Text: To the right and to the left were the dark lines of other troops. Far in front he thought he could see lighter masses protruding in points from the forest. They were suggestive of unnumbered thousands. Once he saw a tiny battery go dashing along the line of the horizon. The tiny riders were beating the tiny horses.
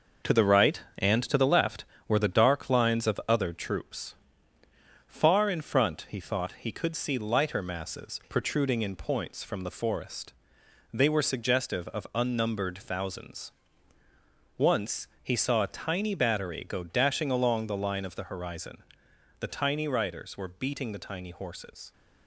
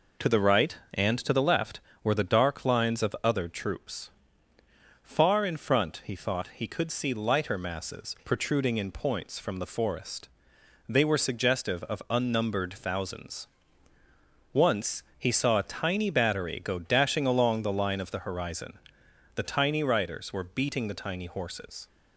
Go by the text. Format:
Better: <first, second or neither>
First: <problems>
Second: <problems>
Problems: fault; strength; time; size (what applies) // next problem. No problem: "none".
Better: second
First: gets quieter; noticeable; throughout; 5.5 dB // pauses between "Once" and "he"; slight; at 15.0 s; 0.16 s long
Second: pauses between "Once" and "he"; slight; at 15.0 s; 0.16 s long